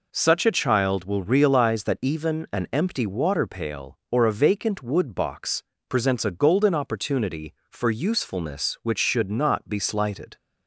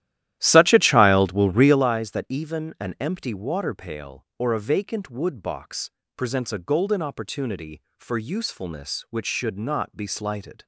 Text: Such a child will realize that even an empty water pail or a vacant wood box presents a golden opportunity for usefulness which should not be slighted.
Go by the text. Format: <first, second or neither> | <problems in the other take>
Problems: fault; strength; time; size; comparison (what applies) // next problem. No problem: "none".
first | starts louder than the rest; strong; until 1.9 s; 13.5 dB // pauses between "box" and "presents"; slight; at 5.8 s; 0.26 s long; slight in the first